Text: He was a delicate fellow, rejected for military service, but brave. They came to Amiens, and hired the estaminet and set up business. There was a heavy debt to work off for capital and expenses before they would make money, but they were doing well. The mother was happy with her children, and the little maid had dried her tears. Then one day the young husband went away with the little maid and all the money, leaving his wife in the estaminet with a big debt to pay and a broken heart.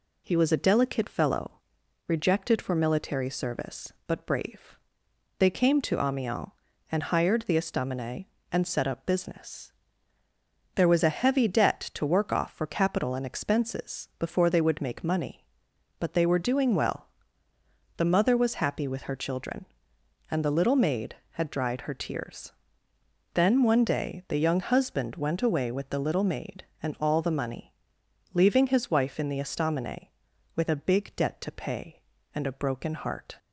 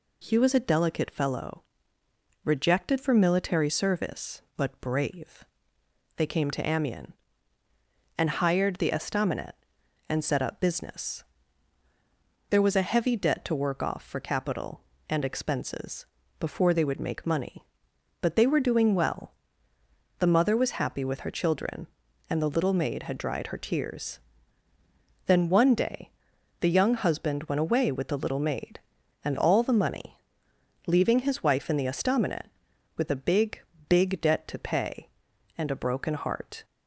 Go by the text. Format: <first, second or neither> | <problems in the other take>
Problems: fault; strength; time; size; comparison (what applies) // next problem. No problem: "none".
first | pauses between "expenses" and "before"; slight; at 16.0 s; 0.32 s long // pauses between "day" and "the"; noticeable; at 26.1 s; 0.50 s long // says "big" twice; at 33.8 s